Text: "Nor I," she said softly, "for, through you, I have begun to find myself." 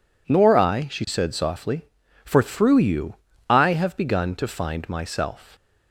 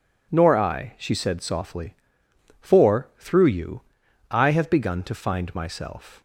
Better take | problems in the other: neither | none

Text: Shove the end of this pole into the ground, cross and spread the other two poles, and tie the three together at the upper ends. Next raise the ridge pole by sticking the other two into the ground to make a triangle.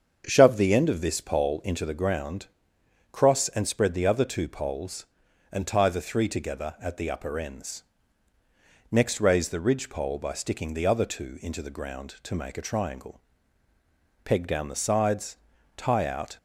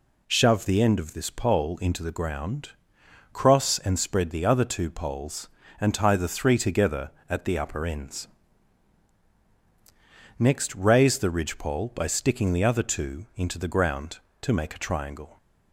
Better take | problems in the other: second | starts louder than the rest; strong; until 1.2 s; 7 dB // goes on to say "Peg down the sides tie out"; strong; from 14.2 s on; 2.1 s long

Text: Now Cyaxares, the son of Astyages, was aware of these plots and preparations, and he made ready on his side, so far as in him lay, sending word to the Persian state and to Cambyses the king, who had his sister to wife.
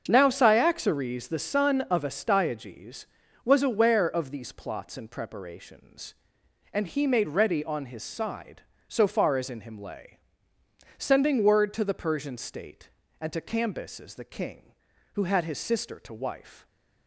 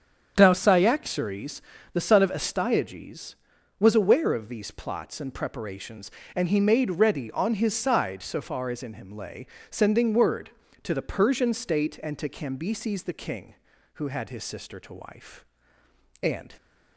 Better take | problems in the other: first | starts louder than the rest; strong; until 1.3 s; 8 dB; also in the first // goes on to say "And"; slight; from 16.2 s on; 0.32 s long

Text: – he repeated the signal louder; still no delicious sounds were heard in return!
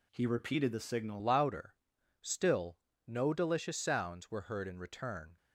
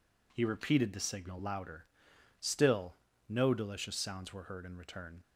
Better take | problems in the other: second | changes voice at "louder"; from 1.2 s on; 4.1 s long // pauses between "still" and "no"; slight; at 2.7 s; 0.30 s long; slight in the second

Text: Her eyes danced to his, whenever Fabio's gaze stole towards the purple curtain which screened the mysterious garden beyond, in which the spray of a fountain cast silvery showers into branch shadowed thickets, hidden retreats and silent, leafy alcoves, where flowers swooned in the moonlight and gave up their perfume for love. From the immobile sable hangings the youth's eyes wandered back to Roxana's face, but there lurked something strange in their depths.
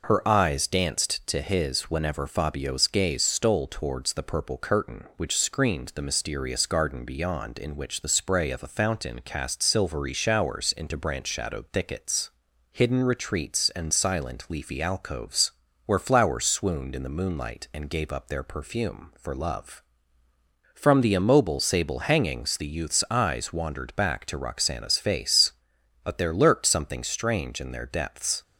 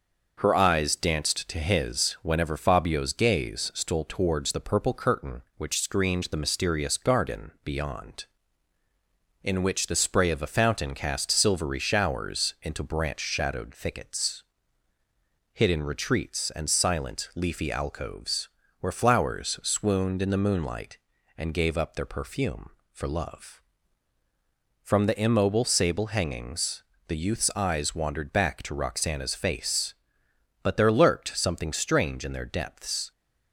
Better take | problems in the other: first | gets quieter; slight; throughout; 2 dB // pauses between "hangings" and "the"; slight; at 26.8 s; 0.24 s long

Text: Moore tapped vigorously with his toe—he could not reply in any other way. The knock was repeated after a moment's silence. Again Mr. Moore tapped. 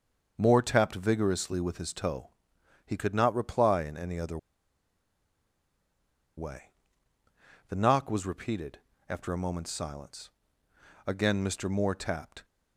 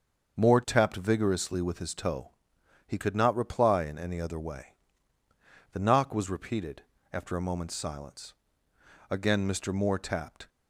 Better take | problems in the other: second | starts louder than the rest; until 1.3 s; 6.5 dB; also in the second // pauses between "other" and "way"; strong; at 4.3 s; 2.0 s long // pauses between "repeated" and "after"; slight; at 8.7 s; 0.30 s long; slight in the second

